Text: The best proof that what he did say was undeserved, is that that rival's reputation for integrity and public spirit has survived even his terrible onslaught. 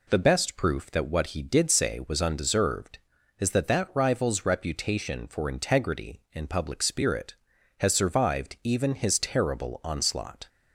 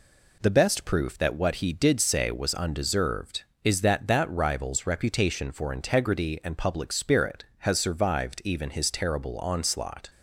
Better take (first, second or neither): neither